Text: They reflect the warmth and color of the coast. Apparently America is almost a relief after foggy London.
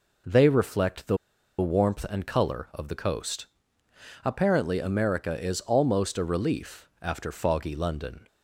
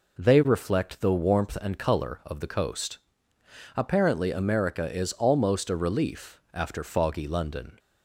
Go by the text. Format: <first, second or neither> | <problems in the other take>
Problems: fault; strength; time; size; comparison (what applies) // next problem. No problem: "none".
second | pauses between "the" and "warmth"; at 1.1 s; 0.43 s long